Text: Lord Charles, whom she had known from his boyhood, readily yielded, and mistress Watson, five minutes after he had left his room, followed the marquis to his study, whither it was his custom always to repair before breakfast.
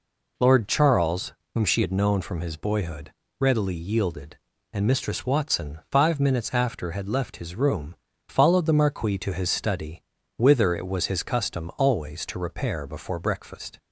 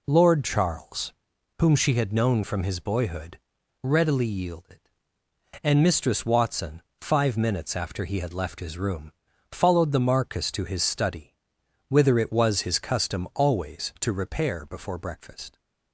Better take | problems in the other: second | skips "he"; at 6.9 s

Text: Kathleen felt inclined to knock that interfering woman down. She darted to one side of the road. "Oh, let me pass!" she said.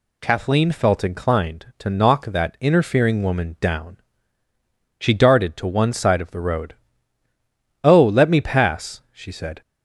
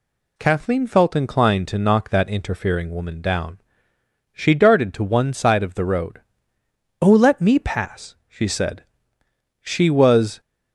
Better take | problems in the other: first | goes on to say "She was"; noticeable; from 9.6 s on; 0.78 s long

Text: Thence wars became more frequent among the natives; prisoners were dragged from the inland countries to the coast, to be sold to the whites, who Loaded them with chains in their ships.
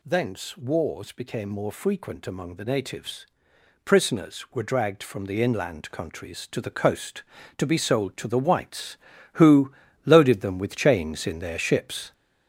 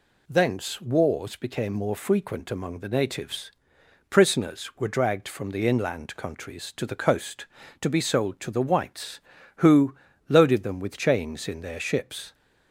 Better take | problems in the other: second | gets louder; noticeable; throughout; 6 dB // pauses between "who" and "Loaded"; slight; at 9.7 s; 0.32 s long; slight in the second

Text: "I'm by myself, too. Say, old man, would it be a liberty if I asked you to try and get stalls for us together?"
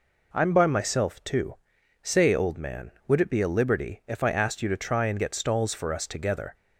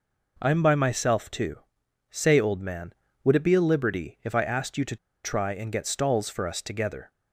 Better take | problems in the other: first | pauses between "to" and "try"; slight; at 4.9 s; 0.28 s long

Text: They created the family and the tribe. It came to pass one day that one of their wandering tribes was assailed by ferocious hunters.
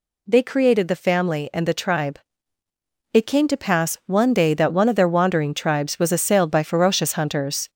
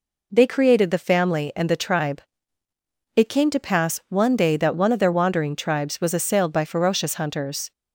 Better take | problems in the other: second | gets louder; slight; throughout; 2.5 dB

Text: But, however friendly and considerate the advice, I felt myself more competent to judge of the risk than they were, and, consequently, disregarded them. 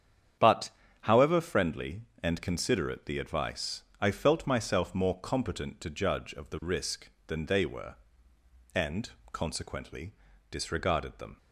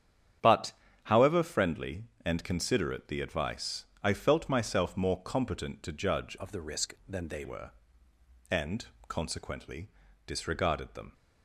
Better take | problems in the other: first | starts louder than the rest; strong; until 1.7 s; 9 dB; strong in the first // changes voice from "of" to "they"; from 6.3 to 7.4 s; 1.1 s long

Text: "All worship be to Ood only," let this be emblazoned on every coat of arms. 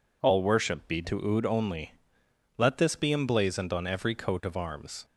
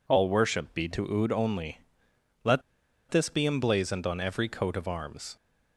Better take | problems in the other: first | pauses between "let" and "this"; noticeable; at 2.6 s; 0.48 s long

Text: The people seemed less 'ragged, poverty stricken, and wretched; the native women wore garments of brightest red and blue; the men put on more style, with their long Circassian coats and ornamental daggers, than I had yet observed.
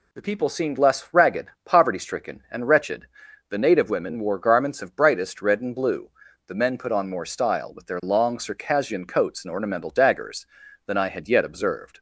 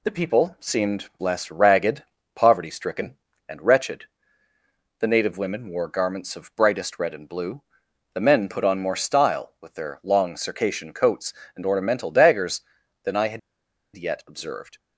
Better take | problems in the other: first | pauses between "had" and "yet"; noticeable; at 13.3 s; 0.55 s long

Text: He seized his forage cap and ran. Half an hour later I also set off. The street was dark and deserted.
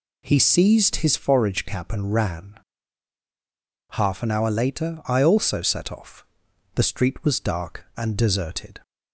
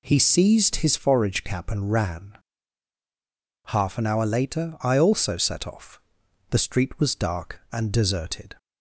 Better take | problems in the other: neither | none

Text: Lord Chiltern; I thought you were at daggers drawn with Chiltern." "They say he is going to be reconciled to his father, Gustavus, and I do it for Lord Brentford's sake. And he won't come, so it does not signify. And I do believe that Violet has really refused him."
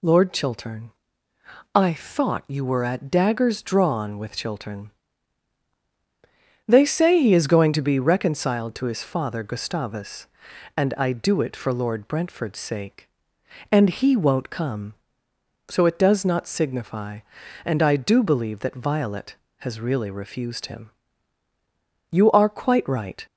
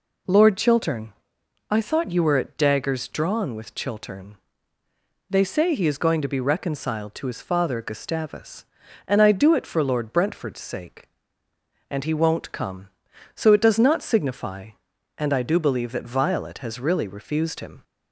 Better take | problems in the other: second | goes on to say "You are quite right"; noticeable; from 22.1 s on; 1.1 s long

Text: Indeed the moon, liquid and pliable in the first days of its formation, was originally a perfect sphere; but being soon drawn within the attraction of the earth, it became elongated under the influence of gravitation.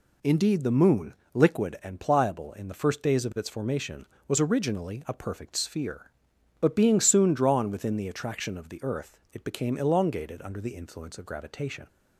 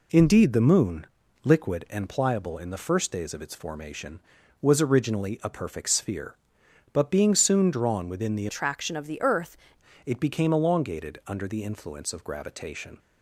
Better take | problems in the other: first | changes voice from "attraction" to "earth"; from 8.4 to 9.5 s; 1.1 s long

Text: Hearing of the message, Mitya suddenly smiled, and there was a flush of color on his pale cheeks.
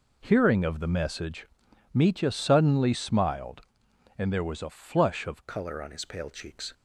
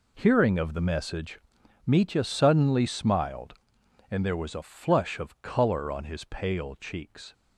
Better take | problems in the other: second | changes voice at "color"; from 5.4 s on; 1.3 s long

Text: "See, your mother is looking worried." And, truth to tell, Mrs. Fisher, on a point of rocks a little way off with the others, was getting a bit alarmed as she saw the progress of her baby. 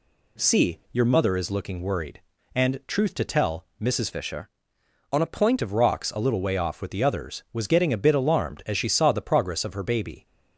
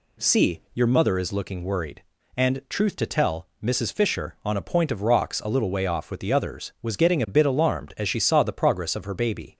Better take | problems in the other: second | changes voice from "Fisher" to "point"; from 4.1 to 5.6 s; 1.5 s long

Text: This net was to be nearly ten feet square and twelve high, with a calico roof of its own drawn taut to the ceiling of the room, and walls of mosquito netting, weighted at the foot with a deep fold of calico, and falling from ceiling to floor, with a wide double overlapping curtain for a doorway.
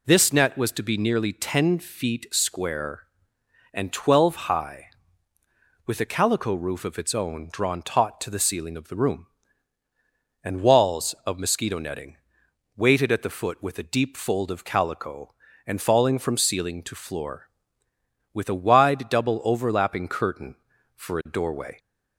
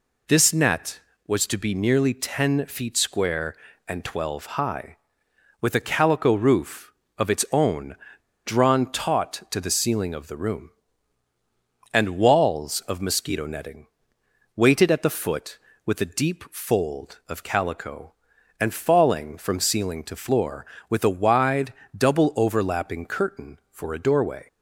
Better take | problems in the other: first | pauses between "own" and "drawn"; noticeable; at 7.9 s; 0.49 s long // pauses between "wide" and "double"; slight; at 21.7 s; 0.22 s long

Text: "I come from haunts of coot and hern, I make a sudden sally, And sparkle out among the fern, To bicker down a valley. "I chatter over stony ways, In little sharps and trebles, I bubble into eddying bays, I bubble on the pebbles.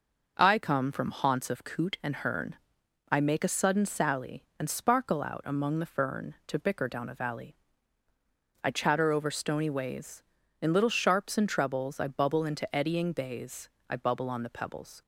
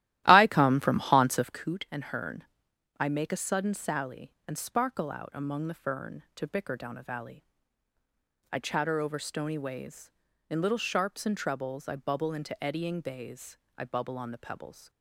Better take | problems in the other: first | starts louder than the rest; strong; until 1.7 s; 14.5 dB

